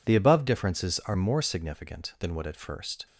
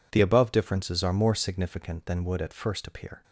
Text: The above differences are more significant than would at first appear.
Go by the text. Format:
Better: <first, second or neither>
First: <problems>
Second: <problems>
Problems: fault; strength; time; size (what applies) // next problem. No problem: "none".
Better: second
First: stops before "appear"; at 3.0 s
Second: none